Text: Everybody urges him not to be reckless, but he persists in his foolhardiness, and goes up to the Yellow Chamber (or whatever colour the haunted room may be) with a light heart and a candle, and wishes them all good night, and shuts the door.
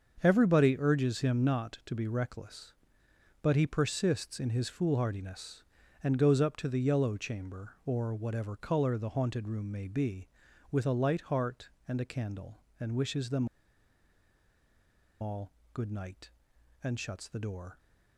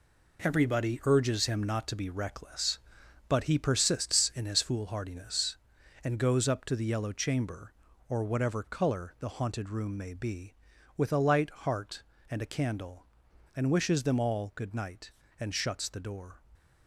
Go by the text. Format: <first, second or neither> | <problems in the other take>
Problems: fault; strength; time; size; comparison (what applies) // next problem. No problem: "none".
second | starts louder than the rest; until 1.2 s; 6.5 dB // pauses between "them" and "all"; strong; at 13.4 s; 1.7 s long // pauses between "all" and "good"; slight; at 15.5 s; 0.22 s long